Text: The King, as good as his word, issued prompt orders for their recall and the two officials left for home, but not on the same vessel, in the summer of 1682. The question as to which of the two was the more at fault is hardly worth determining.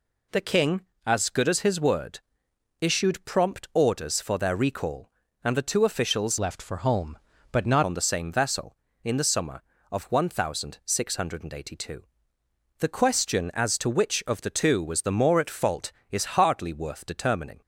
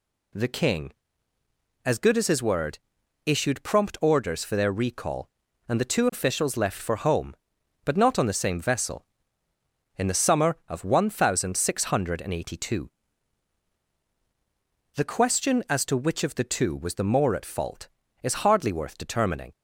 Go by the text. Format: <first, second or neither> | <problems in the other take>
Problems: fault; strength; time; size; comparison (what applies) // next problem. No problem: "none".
second | changes voice from "left" to "not"; from 6.3 to 7.8 s; 1.5 s long